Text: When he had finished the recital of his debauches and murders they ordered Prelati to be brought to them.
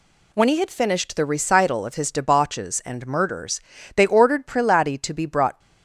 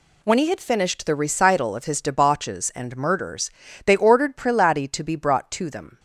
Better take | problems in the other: second | pauses between "murders" and "they"; slight; at 3.5 s; 0.36 s long; slight in the second // stops before "to them"; at 5.5 s

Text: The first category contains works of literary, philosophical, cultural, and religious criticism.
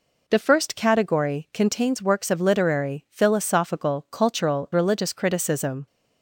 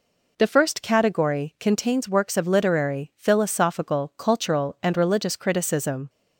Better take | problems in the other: second | skips "and"; at 4.7 s

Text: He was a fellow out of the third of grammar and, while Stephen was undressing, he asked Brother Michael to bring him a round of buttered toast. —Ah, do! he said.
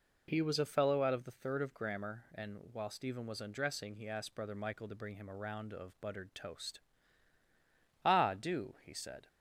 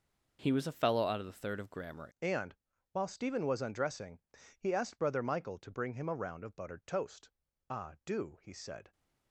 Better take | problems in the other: first | changes voice at "and"; from 2.2 s on; 6.7 s long

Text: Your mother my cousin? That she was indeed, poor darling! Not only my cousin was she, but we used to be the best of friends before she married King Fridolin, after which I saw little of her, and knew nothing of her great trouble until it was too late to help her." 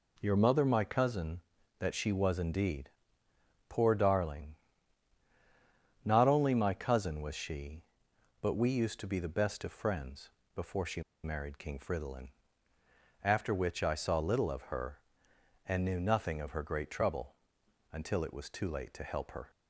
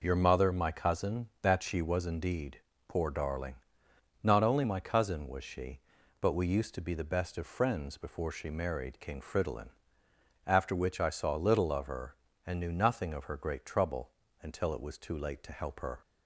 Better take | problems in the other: second | pauses between "friends" and "before"; slight; at 10.2 s; 0.26 s long // pauses between "she" and "married"; slight; at 11.0 s; 0.22 s long // pauses between "trouble" and "until"; noticeable; at 17.3 s; 0.58 s long; slight in the second

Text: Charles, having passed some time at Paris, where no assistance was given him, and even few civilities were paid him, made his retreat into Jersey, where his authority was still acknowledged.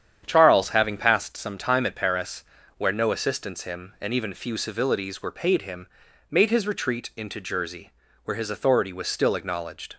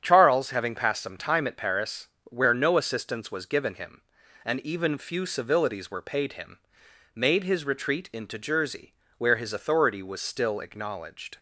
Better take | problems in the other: second | starts louder than the rest; strong; until 1.2 s; 9 dB; strong in the second // skips "was given"; at 3.6 s

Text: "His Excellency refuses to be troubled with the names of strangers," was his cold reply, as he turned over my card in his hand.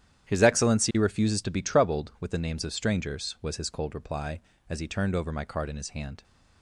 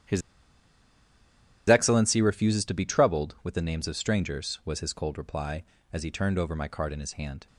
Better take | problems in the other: first | starts louder than the rest; strong; until 2.5 s; 9.5 dB; strong in the first // pauses between "His" and "Excellency"; strong; at 0.2 s; 1.4 s long

